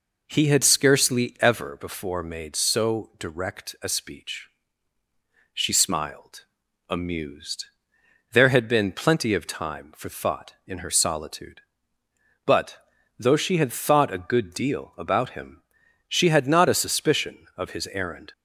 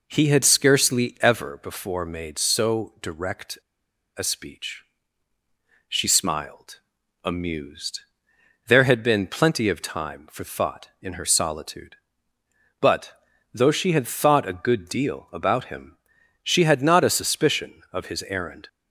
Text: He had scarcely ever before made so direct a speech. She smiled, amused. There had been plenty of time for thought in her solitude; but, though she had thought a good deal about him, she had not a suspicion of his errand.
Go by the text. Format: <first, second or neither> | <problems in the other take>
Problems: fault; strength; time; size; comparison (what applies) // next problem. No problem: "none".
first | pauses between "direct" and "a"; noticeable; at 3.5 s; 0.60 s long